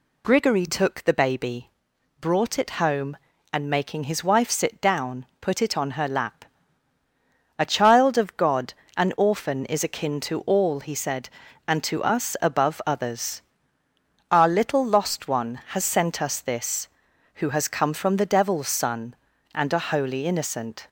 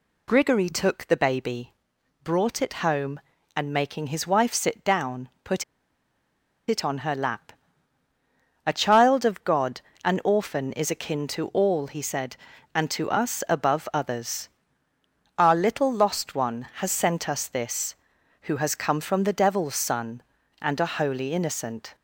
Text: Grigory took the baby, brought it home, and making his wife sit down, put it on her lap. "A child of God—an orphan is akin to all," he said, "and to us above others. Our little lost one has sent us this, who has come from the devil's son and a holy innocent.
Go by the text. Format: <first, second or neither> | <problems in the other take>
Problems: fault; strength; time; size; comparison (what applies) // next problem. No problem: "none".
first | pauses between "put" and "it"; at 5.6 s; 1.0 s long